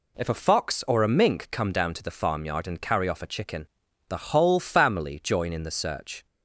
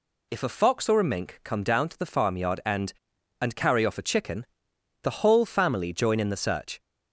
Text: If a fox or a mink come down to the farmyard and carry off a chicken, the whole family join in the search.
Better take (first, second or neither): first